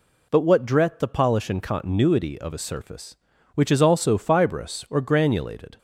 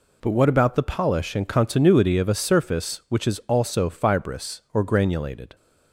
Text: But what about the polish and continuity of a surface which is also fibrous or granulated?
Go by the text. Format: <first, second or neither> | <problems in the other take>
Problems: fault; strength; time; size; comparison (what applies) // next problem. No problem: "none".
second | says "dret" for "about"; at 0.6 s